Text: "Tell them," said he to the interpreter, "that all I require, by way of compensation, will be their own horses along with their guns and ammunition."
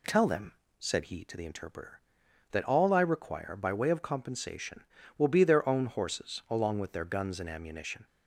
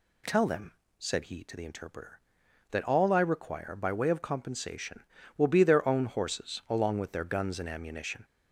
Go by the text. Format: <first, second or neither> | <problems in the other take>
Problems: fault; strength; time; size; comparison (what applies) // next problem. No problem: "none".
first | gets louder; throughout; 4 dB